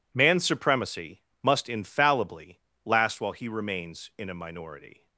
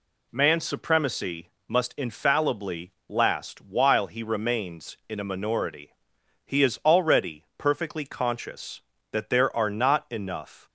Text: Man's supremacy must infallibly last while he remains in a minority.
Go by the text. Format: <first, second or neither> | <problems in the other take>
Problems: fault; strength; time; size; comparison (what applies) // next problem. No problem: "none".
first | pauses between "supremacy" and "must"; slight; at 1.4 s; 0.18 s long; slight in the first // pauses between "infallibly" and "last"; slight; at 2.9 s; 0.16 s long; slight in the first // goes on to say "He is already perfectly conscious that there are not enough"; strong; from 6.4 s on; 4.2 s long